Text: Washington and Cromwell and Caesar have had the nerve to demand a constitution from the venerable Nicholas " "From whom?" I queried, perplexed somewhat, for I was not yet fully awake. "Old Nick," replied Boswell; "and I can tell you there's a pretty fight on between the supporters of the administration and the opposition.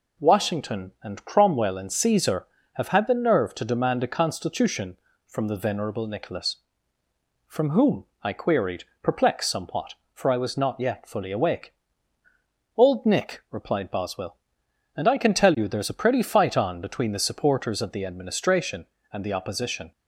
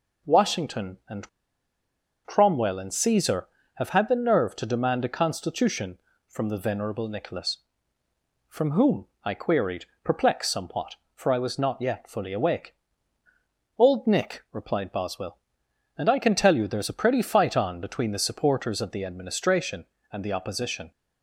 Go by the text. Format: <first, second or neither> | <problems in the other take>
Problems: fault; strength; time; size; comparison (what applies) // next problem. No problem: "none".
first | pauses between "and" and "Cromwell"; noticeable; at 1.2 s; 0.97 s long